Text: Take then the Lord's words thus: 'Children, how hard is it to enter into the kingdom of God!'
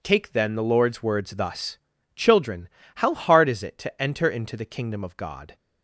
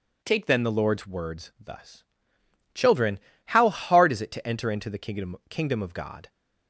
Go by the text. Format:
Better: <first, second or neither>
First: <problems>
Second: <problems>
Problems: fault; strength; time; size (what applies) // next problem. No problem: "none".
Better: first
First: none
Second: says "kingdom" twice; at 5.5 s